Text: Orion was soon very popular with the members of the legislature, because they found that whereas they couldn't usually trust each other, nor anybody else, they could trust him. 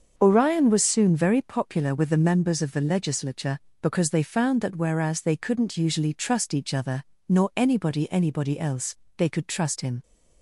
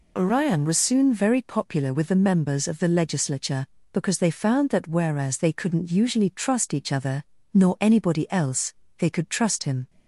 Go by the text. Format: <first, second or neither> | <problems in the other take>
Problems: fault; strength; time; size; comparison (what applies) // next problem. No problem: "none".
second | starts louder than the rest; until 1.1 s; 6.5 dB // says "anybody" twice; at 8.1 s